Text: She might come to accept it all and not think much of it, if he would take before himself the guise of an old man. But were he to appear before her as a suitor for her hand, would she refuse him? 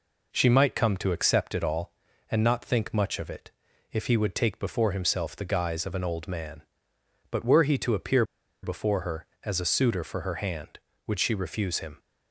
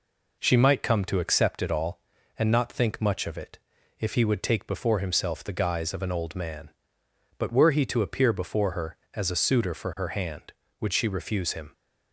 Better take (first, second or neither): second